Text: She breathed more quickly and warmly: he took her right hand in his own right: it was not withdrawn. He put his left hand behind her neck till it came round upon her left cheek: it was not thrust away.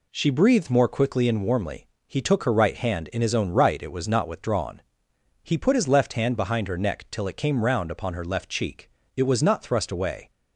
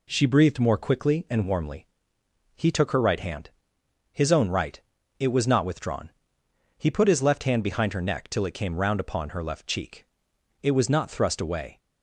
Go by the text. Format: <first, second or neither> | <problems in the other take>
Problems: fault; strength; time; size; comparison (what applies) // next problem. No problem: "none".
first | skips "in"; at 3.8 s